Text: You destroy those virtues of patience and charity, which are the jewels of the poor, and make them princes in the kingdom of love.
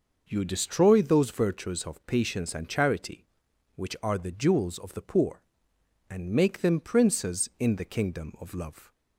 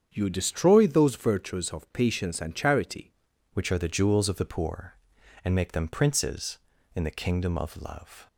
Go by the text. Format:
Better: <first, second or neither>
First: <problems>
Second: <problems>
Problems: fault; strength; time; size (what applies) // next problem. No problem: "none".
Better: first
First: none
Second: starts louder than the rest; strong; until 1.1 s; 8 dB // changes voice at "which"; from 3.5 s on; 4.7 s long